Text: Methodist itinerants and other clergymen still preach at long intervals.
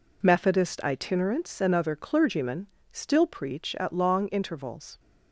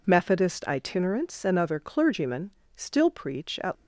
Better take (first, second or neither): first